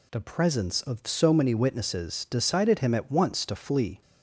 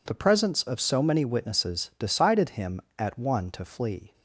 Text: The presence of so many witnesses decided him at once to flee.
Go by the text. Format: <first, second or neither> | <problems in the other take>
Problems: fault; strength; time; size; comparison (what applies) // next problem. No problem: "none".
first | says "one" for "once"; at 3.1 s